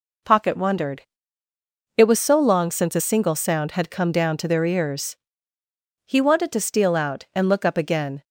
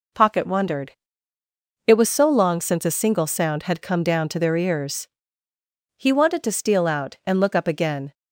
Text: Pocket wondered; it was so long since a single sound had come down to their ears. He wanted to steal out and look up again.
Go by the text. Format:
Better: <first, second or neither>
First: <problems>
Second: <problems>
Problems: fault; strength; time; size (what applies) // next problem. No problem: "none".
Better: neither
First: none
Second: none